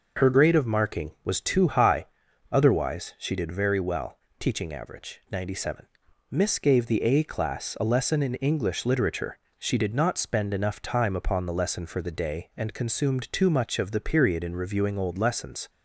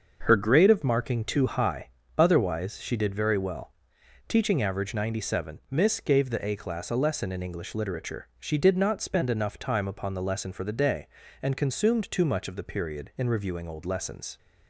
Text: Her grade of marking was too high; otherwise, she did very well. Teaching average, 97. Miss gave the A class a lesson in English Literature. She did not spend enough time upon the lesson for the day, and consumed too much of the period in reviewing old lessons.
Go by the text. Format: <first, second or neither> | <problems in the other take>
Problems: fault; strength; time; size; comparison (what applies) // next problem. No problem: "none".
first | starts louder than the rest; until 1.2 s; 6.5 dB // skips "was"; at 1.2 s